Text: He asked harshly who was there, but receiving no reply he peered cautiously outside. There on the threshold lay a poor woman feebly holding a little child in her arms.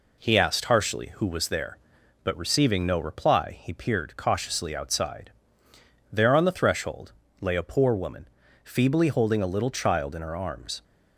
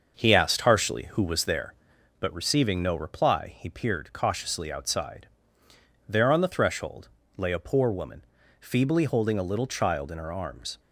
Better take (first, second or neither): first